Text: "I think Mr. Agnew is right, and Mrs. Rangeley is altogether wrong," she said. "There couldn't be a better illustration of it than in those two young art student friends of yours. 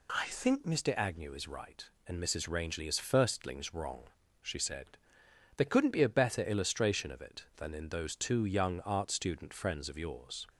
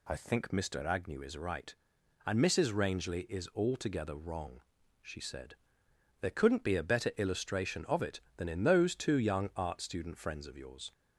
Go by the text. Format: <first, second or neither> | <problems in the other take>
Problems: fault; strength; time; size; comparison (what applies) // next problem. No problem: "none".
second | says "firstlings" for "altogether"; at 2.9 s